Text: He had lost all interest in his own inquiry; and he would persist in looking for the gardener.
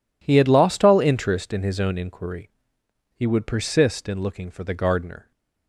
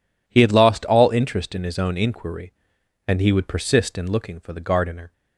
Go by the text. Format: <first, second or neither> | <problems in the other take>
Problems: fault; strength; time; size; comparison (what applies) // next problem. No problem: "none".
second | skips "and"; at 2.8 s